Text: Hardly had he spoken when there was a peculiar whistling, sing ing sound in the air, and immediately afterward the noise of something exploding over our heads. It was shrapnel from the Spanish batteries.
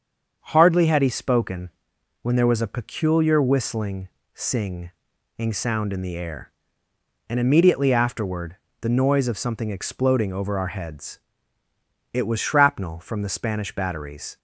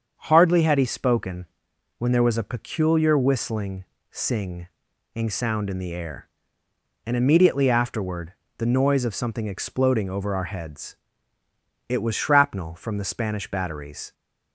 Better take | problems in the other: neither | starts louder than the rest; the same in both // pauses between "spoken" and "when"; noticeable; the same in both // pauses between "sing" and "ing"; noticeable; the same in both // pauses between "afterward" and "the"; slight; the same in both

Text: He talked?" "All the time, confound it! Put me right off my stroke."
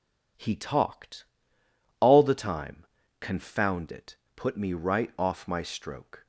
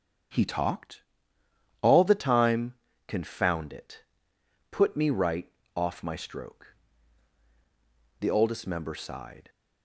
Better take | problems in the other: first | starts louder than the rest; strong; until 2.1 s; 7.5 dB // pauses between "right" and "off"; slight; at 5.5 s; 0.24 s long // goes on to say "The Oldest Member sighed"; noticeable; from 8.2 s on; 1.2 s long

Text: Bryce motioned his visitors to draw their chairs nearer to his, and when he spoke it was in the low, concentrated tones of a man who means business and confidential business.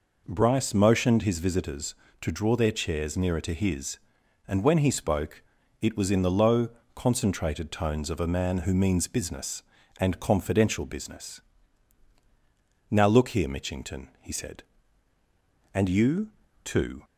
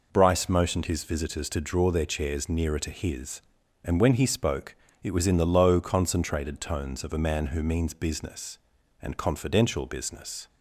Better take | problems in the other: second | pauses between "spoke" and "it"; at 5.4 s; 0.40 s long; slight in the second // goes on to say "Now look here Mitchington he said and you too"; strong; from 12.8 s on; 4.1 s long

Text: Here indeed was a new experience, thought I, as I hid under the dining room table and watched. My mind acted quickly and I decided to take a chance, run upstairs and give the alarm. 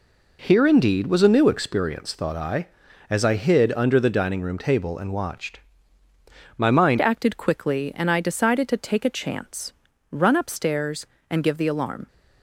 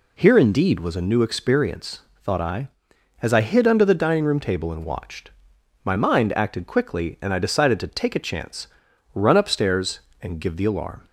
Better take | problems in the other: second | changes voice at "acted"; from 7.0 s on; 5.0 s long

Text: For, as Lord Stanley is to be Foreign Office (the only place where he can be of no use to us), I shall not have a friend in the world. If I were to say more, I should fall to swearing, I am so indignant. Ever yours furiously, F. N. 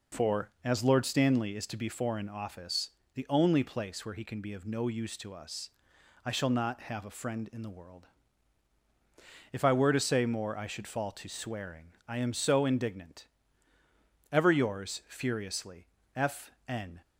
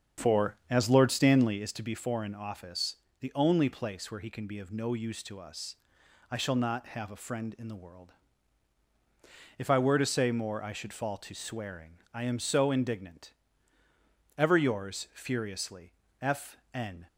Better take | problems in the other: first | starts louder than the rest; strong; until 1.7 s; 7.5 dB // pauses between "F" and "N"; slight; at 16.5 s; 0.16 s long; slight in the first

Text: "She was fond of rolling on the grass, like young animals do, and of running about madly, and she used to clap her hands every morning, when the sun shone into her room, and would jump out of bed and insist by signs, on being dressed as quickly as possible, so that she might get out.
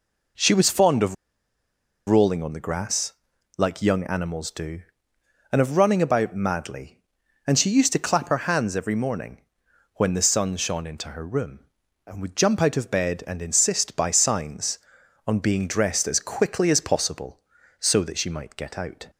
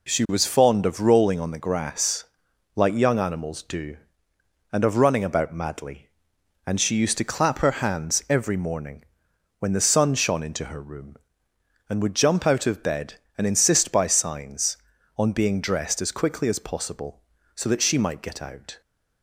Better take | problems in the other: second | pauses between "of" and "rolling"; noticeable; at 1.1 s; 0.93 s long

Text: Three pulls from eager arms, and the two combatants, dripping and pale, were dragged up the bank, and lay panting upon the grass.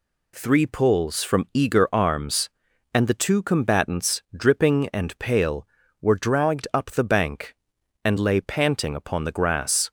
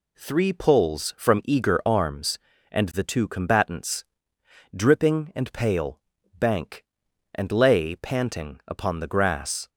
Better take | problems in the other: first | skips "were dragged up the"; at 6.1 s

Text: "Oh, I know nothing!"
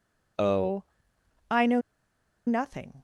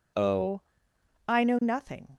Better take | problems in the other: second | pauses between "know" and "nothing"; noticeable; at 1.7 s; 0.67 s long

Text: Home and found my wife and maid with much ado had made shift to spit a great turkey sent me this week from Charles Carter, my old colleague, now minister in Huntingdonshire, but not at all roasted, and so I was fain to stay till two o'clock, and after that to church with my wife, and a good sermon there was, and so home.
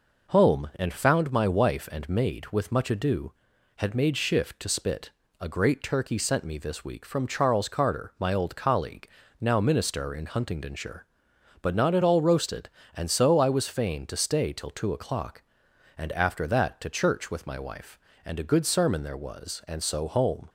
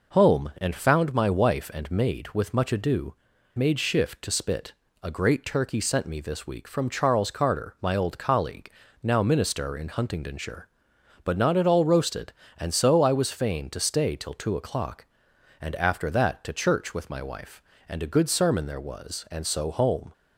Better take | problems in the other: first | skips "had"; at 3.3 s // pauses between "spit" and "a"; slight; at 4.7 s; 0.28 s long; slight in the first

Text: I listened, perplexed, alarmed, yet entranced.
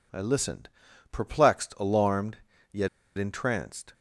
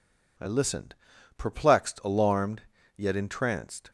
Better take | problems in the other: second | pauses between "yet" and "entranced"; slight; at 2.8 s; 0.30 s long

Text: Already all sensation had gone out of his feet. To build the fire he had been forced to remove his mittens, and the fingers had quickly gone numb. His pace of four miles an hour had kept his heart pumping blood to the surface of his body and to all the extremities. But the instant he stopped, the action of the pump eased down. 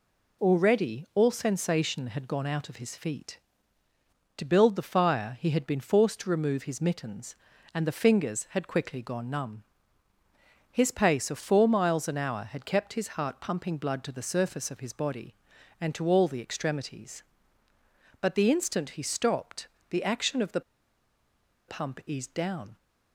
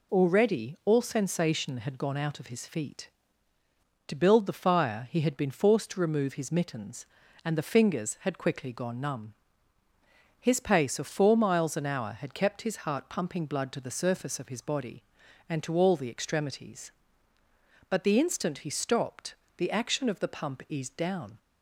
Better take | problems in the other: second | pauses between "the" and "pump"; at 20.6 s; 1.0 s long

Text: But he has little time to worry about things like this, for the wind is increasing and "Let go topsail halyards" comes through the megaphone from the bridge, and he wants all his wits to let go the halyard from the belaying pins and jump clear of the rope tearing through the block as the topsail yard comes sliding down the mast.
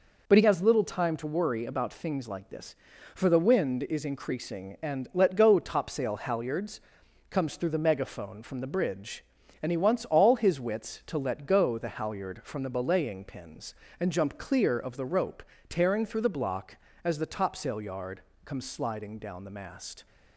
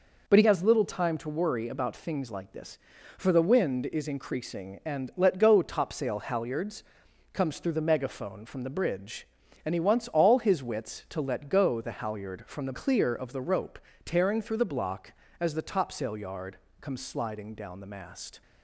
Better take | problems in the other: first | pauses between "halyards" and "comes"; noticeable; at 6.8 s; 0.50 s long; noticeable in the first // skips "belaying pins and jump"; at 12.7 s // pauses between "rope" and "tearing"; slight; at 13.7 s; 0.24 s long; slight in the first // pauses between "yard" and "comes"; slight; at 16.5 s; 0.24 s long; slight in the first

